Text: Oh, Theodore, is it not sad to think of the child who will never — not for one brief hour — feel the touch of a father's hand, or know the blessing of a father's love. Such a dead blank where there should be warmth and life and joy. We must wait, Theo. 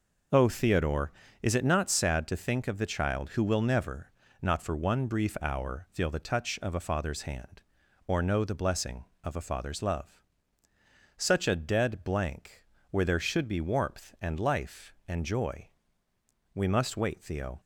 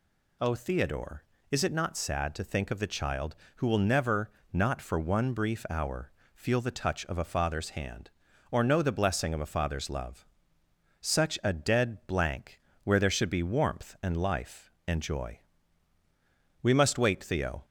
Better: neither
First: pauses between "blank" and "where"; slight; at 12.6 s; 0.30 s long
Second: pauses between "blank" and "where"; slight; at 12.6 s; 0.24 s long

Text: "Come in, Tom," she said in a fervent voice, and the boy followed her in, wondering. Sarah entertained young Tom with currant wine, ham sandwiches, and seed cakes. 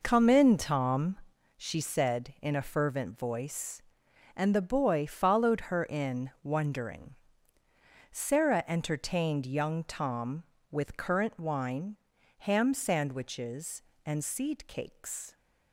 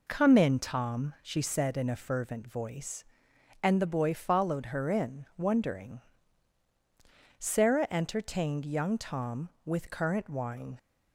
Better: first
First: none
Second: stops before "ham sandwiches and seed cakes"; at 10.7 s

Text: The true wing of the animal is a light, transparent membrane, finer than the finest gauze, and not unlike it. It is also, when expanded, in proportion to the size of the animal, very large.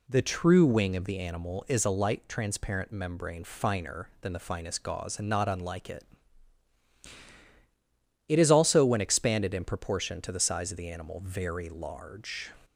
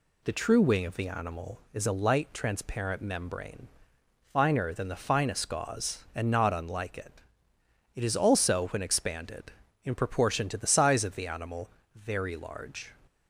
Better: neither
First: none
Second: none

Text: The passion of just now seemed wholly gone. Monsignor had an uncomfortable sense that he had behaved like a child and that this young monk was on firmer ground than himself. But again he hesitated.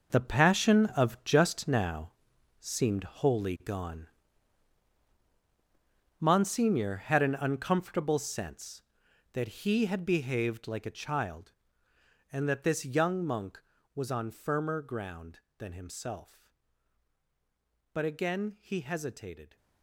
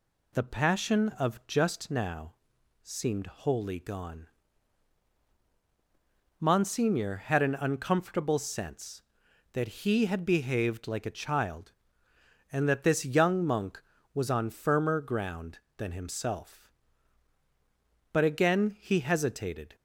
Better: second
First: gets quieter; strong; throughout; 11 dB // pauses between "now" and "seemed"; noticeable; at 2.1 s; 0.48 s long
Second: pauses between "now" and "seemed"; noticeable; at 2.3 s; 0.48 s long

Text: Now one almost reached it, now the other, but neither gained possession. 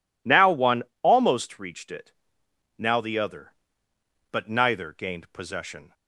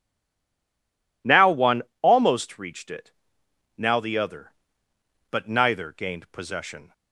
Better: first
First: pauses between "one" and "almost"; slight; at 0.8 s; 0.18 s long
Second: stays silent before the first word; noticeable; until 1.2 s; 1.2 s long // pauses between "one" and "almost"; slight; at 1.8 s; 0.18 s long

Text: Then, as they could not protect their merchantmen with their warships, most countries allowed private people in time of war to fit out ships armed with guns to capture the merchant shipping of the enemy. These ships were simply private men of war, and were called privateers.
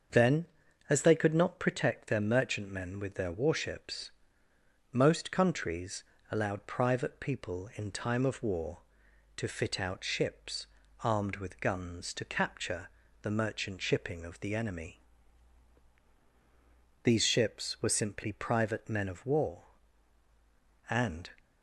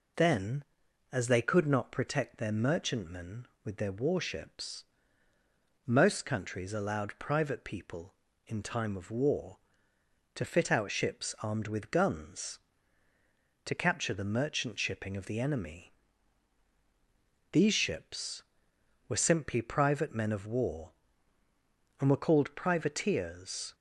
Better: second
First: starts louder than the rest; until 1.5 s; 6.5 dB // pauses between "countries" and "allowed"; slight; at 6.0 s; 0.28 s long // pauses between "ships" and "armed"; slight; at 10.6 s; 0.36 s long // pauses between "capture" and "the"; slight; at 12.8 s; 0.32 s long // stops before "were called privateers"; at 21.3 s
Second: none

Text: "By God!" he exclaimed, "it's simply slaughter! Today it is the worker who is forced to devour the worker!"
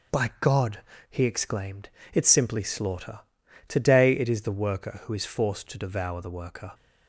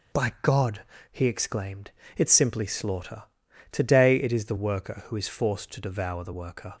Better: neither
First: starts louder than the rest; noticeable; until 1.4 s; 6 dB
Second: starts louder than the rest; until 1.5 s; 6 dB

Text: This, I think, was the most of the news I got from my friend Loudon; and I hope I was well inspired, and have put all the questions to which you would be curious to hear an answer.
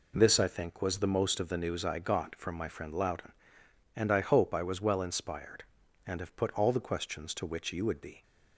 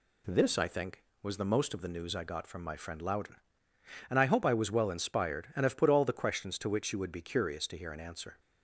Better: second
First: stops before "curious to hear an answer"; at 8.2 s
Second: none

